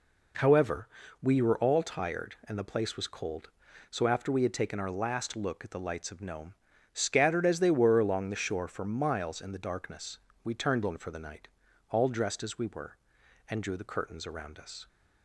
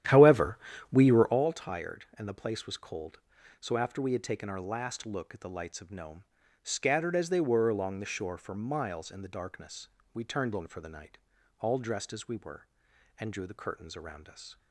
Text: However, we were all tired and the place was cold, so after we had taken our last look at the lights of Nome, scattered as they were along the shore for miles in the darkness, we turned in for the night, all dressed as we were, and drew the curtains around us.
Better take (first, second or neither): first